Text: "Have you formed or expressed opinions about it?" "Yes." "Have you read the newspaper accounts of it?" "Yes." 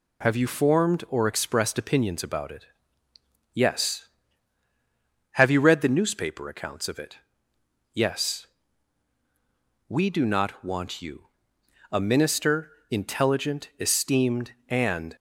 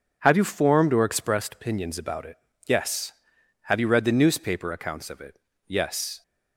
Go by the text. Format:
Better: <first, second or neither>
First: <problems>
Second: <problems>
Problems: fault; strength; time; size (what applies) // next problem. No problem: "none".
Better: second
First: goes on to say "We do not want you A minister intelligent esteemed and"; strong; from 9.8 s on; 5.2 s long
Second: none